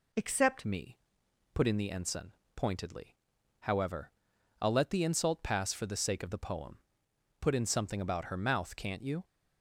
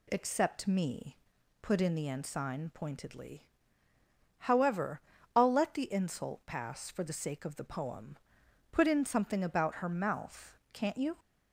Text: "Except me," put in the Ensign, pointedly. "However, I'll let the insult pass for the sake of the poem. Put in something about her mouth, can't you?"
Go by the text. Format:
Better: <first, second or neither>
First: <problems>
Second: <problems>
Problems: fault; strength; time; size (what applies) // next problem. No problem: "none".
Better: second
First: changes voice at "me"; from 0.6 s on; 8.6 s long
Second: none